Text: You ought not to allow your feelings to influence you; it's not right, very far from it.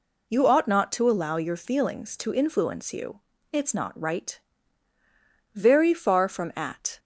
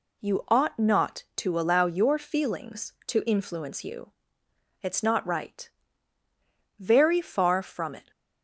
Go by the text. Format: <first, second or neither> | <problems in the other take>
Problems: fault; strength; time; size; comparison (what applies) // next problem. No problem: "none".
second | says "at" for "it"; at 6.5 s